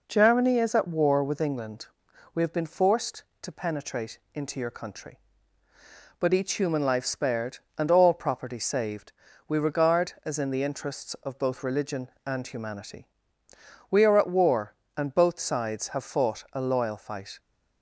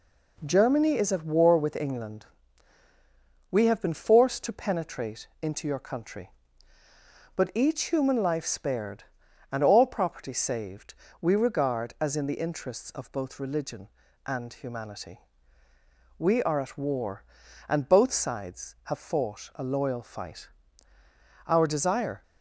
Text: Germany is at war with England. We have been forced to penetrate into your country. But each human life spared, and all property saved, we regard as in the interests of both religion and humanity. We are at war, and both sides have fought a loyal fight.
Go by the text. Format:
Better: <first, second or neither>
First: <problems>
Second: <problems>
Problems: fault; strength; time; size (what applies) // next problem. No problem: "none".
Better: first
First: pauses between "penetrate" and "into"; slight; at 4.1 s; 0.16 s long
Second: pauses between "penetrate" and "into"; slight; at 5.2 s; 0.16 s long // goes on to say "Our desire"; noticeable; from 21.4 s on; 0.74 s long